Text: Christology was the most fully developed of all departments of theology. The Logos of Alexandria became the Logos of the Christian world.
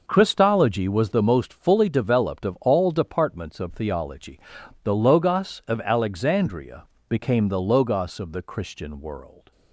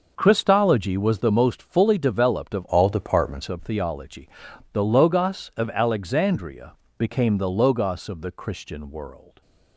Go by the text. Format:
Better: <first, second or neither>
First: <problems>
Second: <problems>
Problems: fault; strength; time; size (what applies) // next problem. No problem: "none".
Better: first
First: pauses between "Alexandria" and "became"; slight; at 6.8 s; 0.24 s long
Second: changes voice from "all" to "departments"; from 2.6 to 3.4 s; 0.8 s long // pauses between "Alexandria" and "became"; slight; at 6.7 s; 0.24 s long